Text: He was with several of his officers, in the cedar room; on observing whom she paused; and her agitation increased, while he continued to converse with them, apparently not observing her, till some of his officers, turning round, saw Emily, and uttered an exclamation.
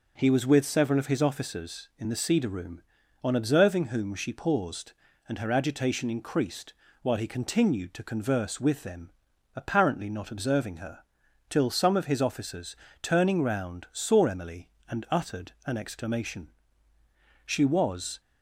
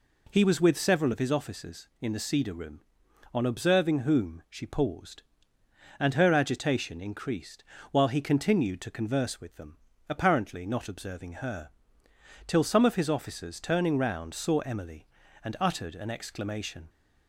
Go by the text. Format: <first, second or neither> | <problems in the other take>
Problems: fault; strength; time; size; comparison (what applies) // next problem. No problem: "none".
second | goes on to say "She was"; noticeable; from 17.4 s on; 0.76 s long